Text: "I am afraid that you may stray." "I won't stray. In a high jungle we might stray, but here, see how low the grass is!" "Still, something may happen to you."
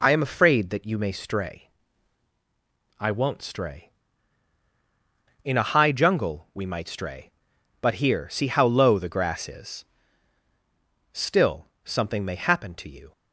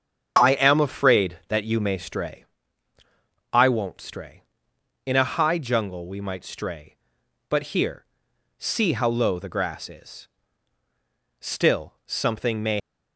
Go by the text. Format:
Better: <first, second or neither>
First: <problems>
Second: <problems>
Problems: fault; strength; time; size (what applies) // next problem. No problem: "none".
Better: first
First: none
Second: starts louder than the rest; until 1.4 s; 7 dB // stops before "happen to you"; at 12.8 s